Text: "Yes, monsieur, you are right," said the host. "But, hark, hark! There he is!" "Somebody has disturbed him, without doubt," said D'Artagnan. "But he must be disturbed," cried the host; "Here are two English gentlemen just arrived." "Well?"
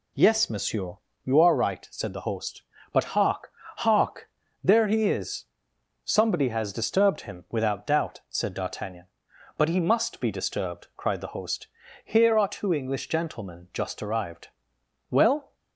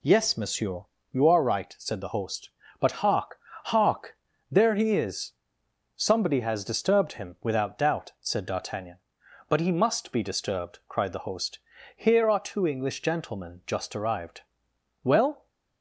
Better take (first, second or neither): neither